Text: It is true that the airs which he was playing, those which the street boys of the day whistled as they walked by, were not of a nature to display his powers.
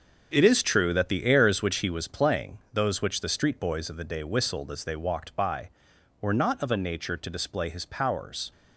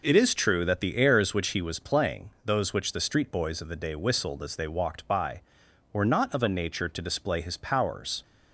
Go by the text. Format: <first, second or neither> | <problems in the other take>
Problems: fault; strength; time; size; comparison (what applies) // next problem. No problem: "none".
second | gets quieter; strong; throughout; 9.5 dB